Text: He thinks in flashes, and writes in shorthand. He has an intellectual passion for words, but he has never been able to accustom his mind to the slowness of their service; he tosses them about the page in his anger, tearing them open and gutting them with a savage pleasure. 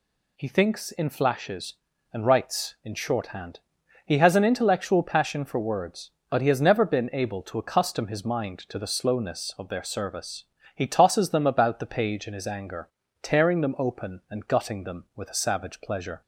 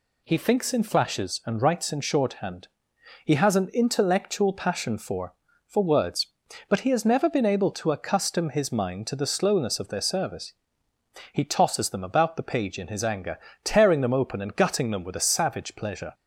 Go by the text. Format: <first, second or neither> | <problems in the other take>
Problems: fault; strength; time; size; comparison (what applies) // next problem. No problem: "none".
first | says "for" twice; at 5.6 s